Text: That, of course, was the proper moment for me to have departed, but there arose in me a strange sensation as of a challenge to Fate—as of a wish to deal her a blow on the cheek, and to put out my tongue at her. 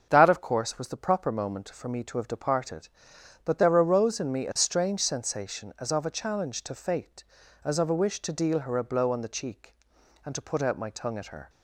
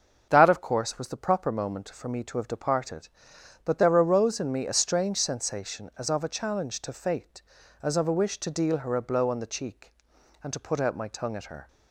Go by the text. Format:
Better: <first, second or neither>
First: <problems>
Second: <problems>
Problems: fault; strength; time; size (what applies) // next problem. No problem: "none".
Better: neither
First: starts louder than the rest; until 1.1 s; 7 dB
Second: starts louder than the rest; until 1.3 s; 7 dB